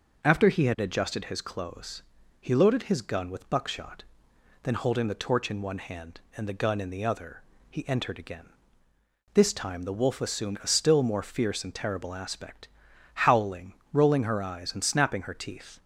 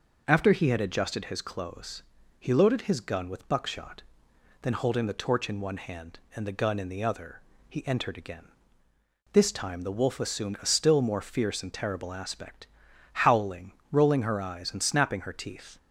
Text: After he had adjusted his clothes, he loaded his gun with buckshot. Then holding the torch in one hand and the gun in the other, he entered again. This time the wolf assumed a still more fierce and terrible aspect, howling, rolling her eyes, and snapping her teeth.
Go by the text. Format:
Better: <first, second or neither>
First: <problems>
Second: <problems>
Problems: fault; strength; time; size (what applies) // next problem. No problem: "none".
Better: neither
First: none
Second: none